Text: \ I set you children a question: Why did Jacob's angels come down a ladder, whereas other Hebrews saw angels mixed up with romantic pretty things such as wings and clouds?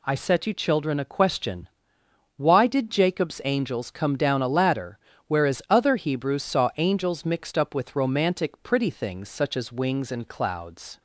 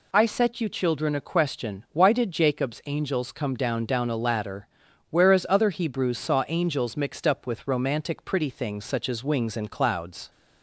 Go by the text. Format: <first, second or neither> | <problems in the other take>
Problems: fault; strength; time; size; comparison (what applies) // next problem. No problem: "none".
first | says "down" twice; at 3.8 s